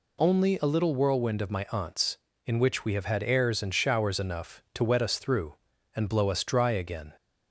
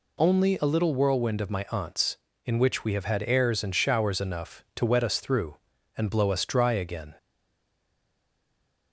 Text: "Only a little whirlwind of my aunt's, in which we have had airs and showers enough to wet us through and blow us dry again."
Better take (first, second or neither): first